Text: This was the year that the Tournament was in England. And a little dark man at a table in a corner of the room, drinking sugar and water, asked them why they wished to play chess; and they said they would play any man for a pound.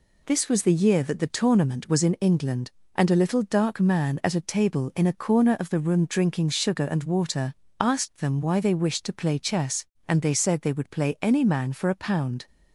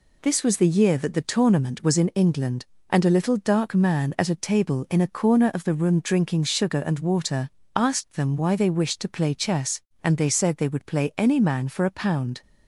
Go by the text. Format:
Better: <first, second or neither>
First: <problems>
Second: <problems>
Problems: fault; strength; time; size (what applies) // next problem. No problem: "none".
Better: neither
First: none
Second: none